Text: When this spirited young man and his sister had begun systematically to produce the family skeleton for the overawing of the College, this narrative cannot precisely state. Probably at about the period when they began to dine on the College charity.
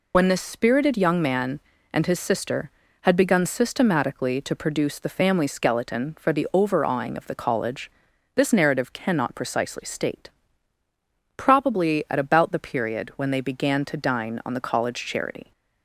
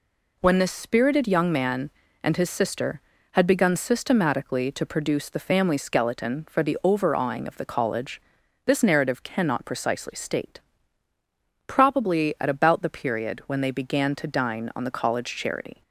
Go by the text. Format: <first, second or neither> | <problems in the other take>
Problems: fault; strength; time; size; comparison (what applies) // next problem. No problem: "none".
second | loses the start of "When"; at 0.1 s; 55 ms